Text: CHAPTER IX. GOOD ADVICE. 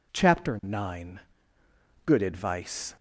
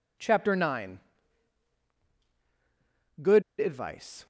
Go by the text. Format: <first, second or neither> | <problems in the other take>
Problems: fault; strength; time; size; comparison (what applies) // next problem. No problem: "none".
first | pauses between "GOOD" and "ADVICE"; slight; at 3.4 s; 0.17 s long